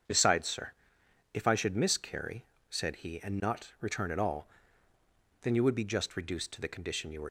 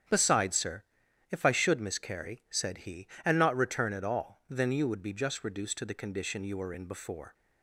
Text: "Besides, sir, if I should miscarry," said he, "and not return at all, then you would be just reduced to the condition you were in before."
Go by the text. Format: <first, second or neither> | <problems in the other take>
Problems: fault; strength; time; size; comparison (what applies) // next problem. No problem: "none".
second | starts louder than the rest; strong; until 1.6 s; 7 dB; strong in the second // stops before "in before"; at 7.2 s